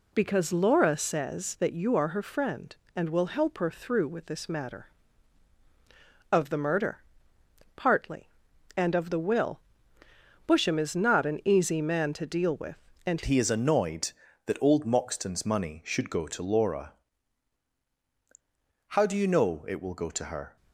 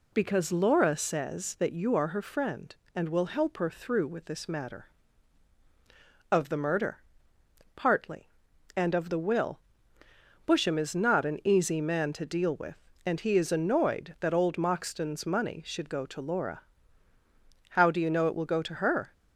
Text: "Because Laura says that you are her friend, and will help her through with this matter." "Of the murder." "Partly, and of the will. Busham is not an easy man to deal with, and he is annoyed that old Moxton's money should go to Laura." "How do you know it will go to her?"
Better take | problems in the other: second | changes voice at "he"; from 13.2 s on; 7.3 s long

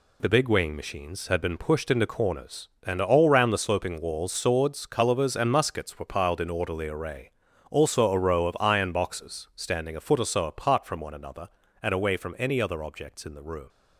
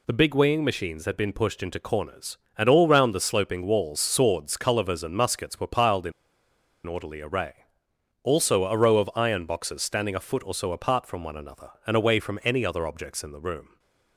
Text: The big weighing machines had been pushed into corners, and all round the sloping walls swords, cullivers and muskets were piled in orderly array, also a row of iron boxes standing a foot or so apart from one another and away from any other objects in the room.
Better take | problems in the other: first | pauses between "in" and "orderly"; noticeable; at 6.1 s; 0.74 s long

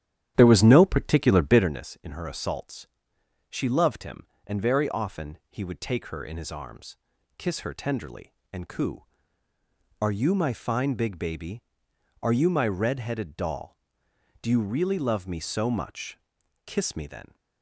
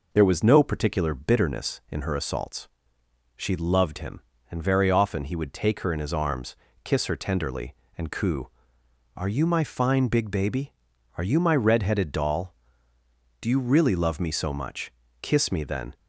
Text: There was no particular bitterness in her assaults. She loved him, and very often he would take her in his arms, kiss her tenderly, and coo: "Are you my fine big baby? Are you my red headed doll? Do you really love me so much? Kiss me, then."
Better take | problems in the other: second | starts louder than the rest; strong; until 1.8 s; 10.5 dB

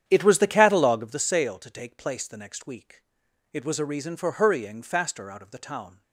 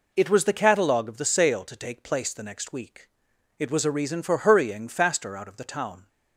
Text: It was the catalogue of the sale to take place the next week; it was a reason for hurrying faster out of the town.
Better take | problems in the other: second | starts louder than the rest; strong; until 1.3 s; 9.5 dB

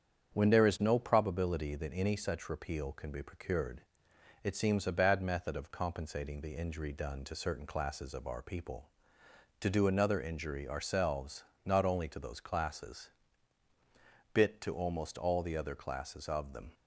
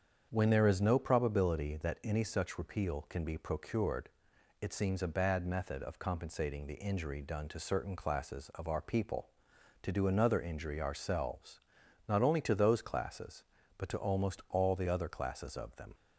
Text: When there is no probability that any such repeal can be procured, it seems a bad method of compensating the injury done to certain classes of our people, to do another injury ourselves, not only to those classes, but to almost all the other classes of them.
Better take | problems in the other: second | starts louder than the rest; strong; until 1.3 s; 8 dB; strong in the second // says "bit" for "but"; at 14.3 s

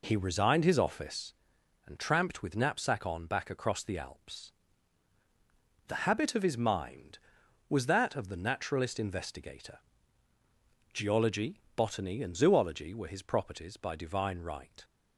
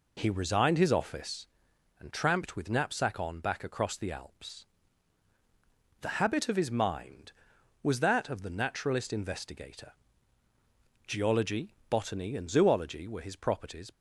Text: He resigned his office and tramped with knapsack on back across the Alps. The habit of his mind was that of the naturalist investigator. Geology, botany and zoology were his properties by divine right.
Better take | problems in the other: first | stops before "by divine right"; at 13.9 s

